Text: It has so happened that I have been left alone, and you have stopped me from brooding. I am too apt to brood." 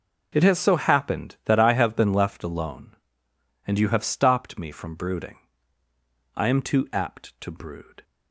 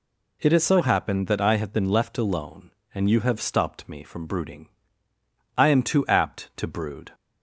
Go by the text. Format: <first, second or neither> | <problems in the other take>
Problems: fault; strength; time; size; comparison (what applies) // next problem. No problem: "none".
neither | none